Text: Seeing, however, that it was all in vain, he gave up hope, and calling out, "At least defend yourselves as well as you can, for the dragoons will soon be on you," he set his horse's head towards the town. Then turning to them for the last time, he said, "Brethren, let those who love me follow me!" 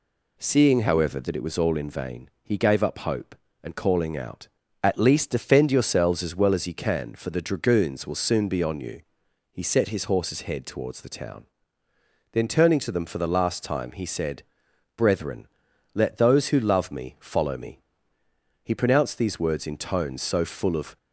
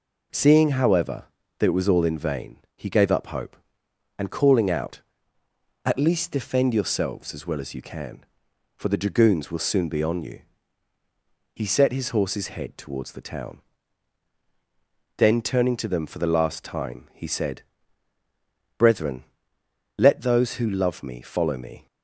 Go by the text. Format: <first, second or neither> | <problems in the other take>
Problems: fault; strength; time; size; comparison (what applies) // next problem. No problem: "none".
second | goes on to say "He pronounced these words in tones so full of"; strong; from 18.6 s on; 2.3 s long